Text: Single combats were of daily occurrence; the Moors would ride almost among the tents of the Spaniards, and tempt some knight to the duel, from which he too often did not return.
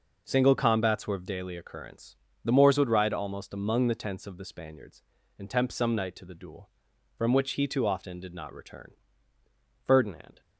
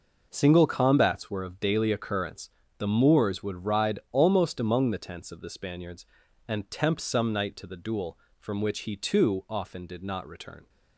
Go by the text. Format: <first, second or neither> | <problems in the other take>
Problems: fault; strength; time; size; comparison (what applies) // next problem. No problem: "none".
second | goes on to say "Ferdinand"; from 9.8 s on; 0.58 s long